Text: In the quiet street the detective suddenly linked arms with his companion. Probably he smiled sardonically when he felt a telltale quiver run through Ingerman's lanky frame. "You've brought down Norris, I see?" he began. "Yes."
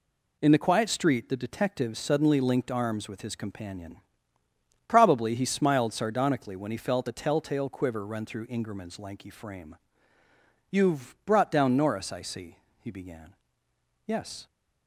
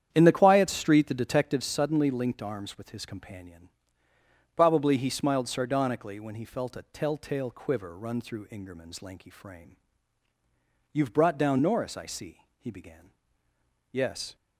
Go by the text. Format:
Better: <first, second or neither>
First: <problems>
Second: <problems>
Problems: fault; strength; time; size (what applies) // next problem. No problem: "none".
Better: first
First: none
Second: starts louder than the rest; strong; until 1.7 s; 9 dB